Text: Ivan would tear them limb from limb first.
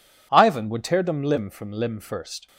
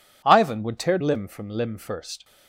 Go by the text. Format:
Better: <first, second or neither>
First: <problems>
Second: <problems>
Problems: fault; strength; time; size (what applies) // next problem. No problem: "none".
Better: first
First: none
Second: skips "them"; at 0.9 s